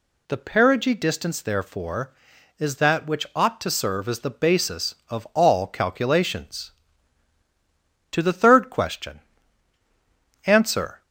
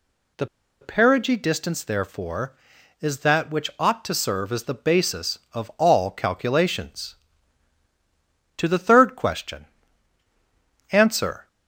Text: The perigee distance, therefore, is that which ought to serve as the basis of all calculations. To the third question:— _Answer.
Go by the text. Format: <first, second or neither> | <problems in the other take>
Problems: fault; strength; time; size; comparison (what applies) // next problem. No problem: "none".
first | pauses between "The" and "perigee"; slight; at 0.4 s; 0.34 s long